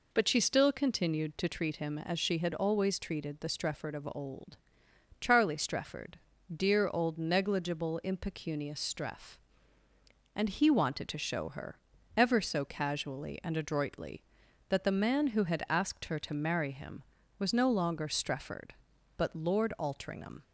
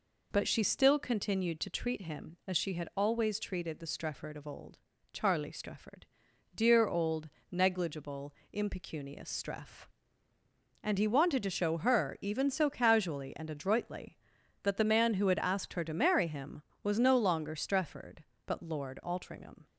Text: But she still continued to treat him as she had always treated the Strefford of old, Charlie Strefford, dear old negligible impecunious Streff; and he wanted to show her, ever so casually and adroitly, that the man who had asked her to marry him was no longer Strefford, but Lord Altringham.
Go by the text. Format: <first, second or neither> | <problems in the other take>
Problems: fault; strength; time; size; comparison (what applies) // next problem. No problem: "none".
first | pauses between "old" and "negligible"; slight; at 7.2 s; 0.20 s long // pauses between "negligible" and "impecunious"; slight; at 8.3 s; 0.20 s long // says "even" for "ever"; at 12.2 s